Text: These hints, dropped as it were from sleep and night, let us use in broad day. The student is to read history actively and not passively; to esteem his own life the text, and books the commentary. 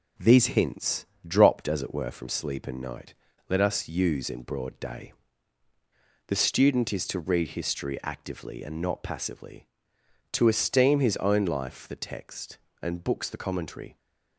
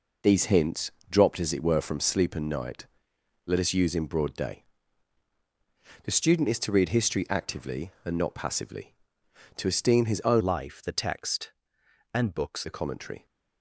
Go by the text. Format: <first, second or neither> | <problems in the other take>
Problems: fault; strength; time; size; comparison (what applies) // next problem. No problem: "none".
first | changes voice from "life" to "books"; from 10.3 to 12.6 s; 2.3 s long